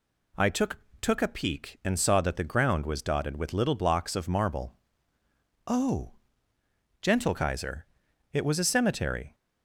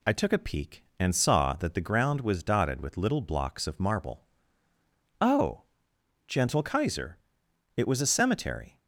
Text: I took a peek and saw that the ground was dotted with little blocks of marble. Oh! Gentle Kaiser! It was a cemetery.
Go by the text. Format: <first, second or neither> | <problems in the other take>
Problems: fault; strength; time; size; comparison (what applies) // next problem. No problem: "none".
second | says "took" twice; at 1.0 s